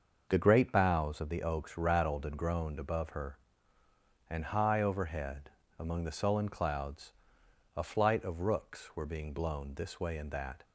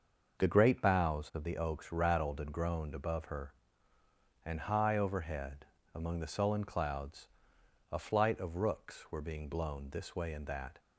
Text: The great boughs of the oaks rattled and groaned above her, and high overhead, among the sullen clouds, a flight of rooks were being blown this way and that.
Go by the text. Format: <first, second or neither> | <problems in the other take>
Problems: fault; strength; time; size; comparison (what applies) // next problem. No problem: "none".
neither | starts louder than the rest; the same in both